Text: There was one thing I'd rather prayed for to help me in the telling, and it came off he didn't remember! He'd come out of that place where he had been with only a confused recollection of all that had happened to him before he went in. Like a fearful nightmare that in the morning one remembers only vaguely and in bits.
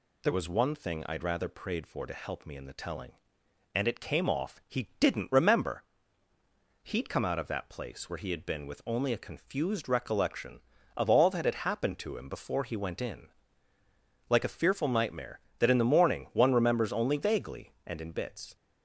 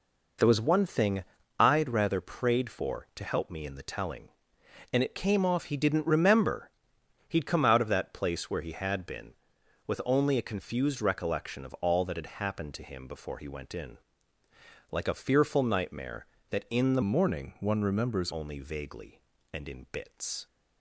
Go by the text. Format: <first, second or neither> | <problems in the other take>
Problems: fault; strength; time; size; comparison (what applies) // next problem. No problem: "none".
first | pauses between "thing" and "I'd"; slight; at 1.2 s; 0.36 s long // changes voice from "morning" to "remembers"; from 17.0 to 18.3 s; 1.3 s long